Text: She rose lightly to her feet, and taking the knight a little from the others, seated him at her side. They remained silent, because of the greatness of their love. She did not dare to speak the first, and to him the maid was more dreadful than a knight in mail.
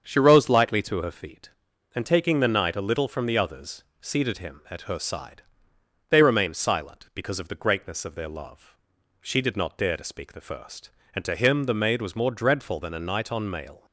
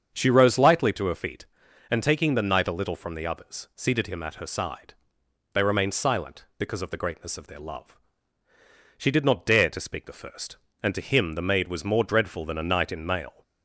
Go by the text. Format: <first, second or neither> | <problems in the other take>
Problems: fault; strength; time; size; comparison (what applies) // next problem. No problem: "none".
second | starts louder than the rest; strong; until 1.0 s; 7 dB; strong in the second // says "on" for "in"; at 13.3 s